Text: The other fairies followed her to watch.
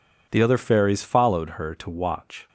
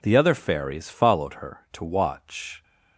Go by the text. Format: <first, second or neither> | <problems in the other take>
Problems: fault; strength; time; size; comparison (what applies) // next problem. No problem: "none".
neither | none